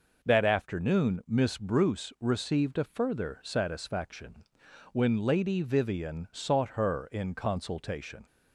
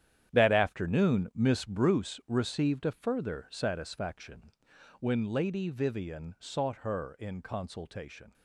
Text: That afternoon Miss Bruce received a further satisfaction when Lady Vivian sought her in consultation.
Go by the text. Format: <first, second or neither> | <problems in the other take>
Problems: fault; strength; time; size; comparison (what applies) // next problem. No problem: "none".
first | gets quieter; strong; throughout; 12 dB // pauses between "satisfaction" and "when"; noticeable; at 4.5 s; 0.48 s long; noticeable in the first